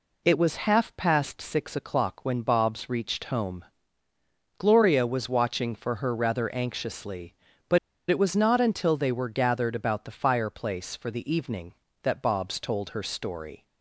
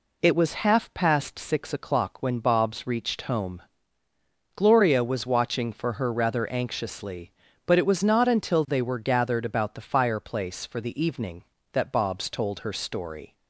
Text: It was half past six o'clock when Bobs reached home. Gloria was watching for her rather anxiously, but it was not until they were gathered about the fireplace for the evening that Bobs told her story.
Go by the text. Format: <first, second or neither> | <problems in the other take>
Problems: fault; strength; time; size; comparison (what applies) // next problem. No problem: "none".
second | pauses between "but" and "it"; slight; at 7.7 s; 0.32 s long